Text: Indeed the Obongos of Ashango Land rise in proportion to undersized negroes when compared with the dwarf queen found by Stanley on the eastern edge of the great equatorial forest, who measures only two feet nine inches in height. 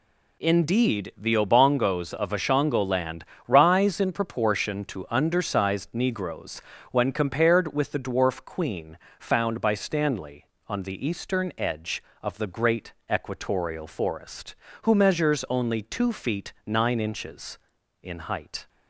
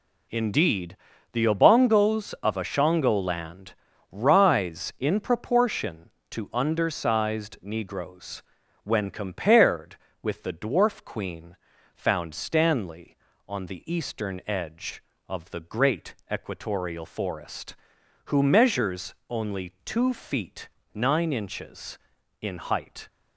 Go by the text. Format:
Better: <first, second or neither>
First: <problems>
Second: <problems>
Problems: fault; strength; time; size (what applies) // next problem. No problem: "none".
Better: first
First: pauses between "Land" and "rise"; slight; at 3.2 s; 0.24 s long // pauses between "negroes" and "when"; slight; at 6.6 s; 0.30 s long // pauses between "queen" and "found"; slight; at 8.9 s; 0.20 s long // pauses between "great" and "equatorial"; slight; at 12.9 s; 0.18 s long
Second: pauses between "Indeed" and "the"; slight; at 0.9 s; 0.36 s long // pauses between "Land" and "rise"; slight; at 3.7 s; 0.36 s long // pauses between "negroes" and "when"; at 8.4 s; 0.42 s long // pauses between "queen" and "found"; at 11.5 s; 0.38 s long // skips "by"; at 12.3 s // pauses between "great" and "equatorial"; slight; at 16.1 s; 0.18 s long // pauses between "measures" and "only"; slight; at 19.1 s; 0.16 s long // pauses between "feet" and "nine"; slight; at 20.6 s; 0.26 s long